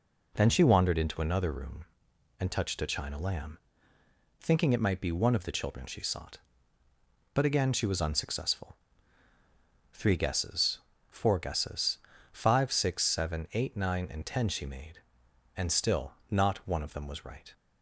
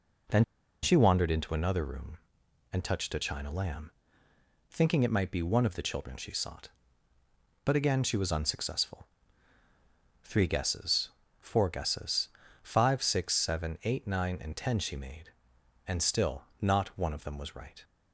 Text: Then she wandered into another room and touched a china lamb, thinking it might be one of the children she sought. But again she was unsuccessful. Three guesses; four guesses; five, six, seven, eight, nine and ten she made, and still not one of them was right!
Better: first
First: pauses between "still" and "not"; slight; at 16.1 s; 0.18 s long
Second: pauses between "Then" and "she"; at 0.4 s; 0.39 s long // pauses between "still" and "not"; slight; at 16.4 s; 0.18 s long

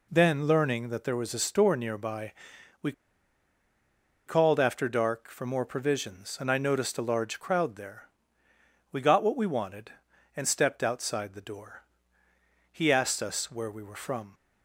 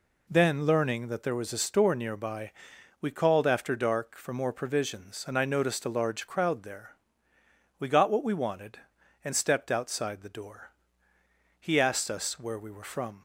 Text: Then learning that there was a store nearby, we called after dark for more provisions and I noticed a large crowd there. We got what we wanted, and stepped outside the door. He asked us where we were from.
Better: second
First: pauses between "we" and "called"; strong; at 2.9 s; 1.3 s long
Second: none

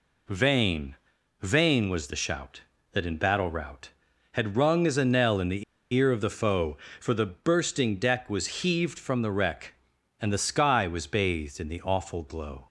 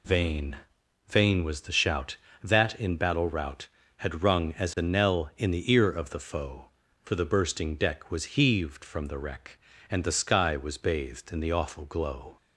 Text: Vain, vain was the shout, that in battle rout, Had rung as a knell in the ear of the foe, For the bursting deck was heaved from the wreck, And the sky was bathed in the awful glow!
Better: second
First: pauses between "the" and "ear"; slight; at 5.6 s; 0.30 s long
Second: none

